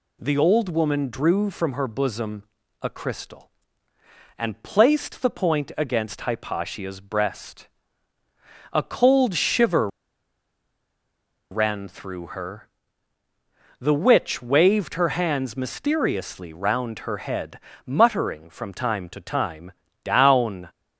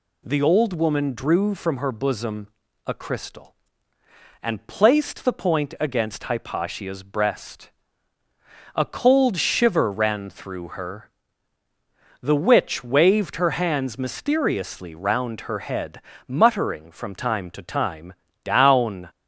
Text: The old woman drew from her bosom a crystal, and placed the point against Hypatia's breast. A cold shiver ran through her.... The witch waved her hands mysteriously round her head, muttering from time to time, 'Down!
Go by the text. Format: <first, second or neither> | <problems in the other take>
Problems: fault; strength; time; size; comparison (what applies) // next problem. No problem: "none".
second | pauses between "bosom" and "a"; at 2.4 s; 0.38 s long; also in the second // pauses between "shiver" and "ran"; strong; at 9.8 s; 1.6 s long